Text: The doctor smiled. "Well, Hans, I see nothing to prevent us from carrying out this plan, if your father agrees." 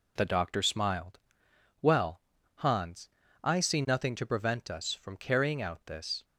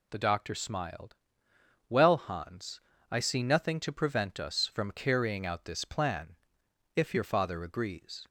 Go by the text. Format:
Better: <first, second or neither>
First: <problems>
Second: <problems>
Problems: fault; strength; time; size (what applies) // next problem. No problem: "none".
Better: second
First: stops before "plan if your father agrees"; at 6.2 s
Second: none